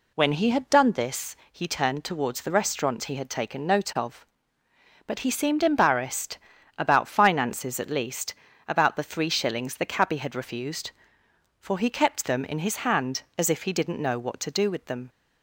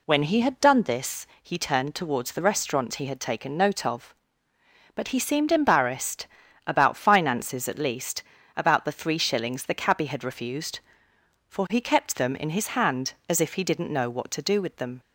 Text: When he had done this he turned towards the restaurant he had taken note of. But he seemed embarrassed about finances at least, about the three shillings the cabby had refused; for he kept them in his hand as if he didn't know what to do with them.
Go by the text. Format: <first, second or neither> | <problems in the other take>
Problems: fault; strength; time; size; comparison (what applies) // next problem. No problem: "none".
neither | pauses between "this" and "he"; slight; the same in both // pauses between "embarrassed" and "about"; the same in both